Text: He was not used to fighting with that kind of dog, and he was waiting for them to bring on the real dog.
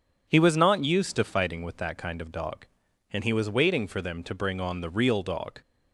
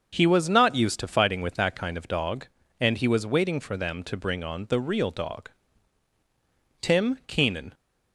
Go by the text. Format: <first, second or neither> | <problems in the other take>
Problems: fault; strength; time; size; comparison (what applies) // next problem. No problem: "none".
first | starts louder than the rest; until 1.1 s; 6.5 dB // goes on to say "Tim Keenan"; noticeable; from 6.8 s on; 0.92 s long